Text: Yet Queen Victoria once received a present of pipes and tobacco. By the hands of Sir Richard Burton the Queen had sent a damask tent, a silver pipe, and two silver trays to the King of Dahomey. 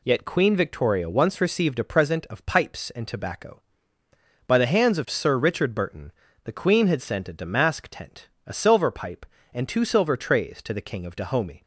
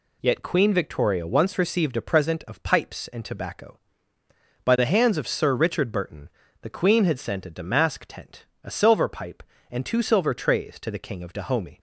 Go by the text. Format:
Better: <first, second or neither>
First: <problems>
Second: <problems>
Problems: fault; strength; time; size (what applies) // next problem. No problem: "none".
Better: neither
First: pauses between "Burton" and "the"; slight; at 6.1 s; 0.32 s long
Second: pauses between "Burton" and "the"; slight; at 6.2 s; 0.32 s long